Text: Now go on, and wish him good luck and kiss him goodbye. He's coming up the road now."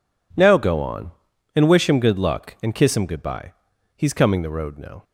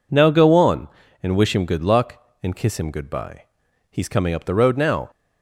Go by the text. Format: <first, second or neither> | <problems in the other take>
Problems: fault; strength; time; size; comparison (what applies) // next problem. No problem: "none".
second | skips "up"; at 4.4 s